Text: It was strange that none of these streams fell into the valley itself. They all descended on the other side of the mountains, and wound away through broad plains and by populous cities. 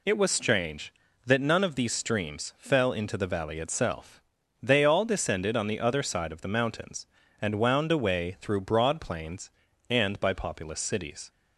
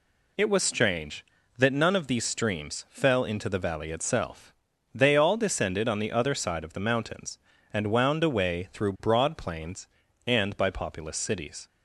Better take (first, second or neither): neither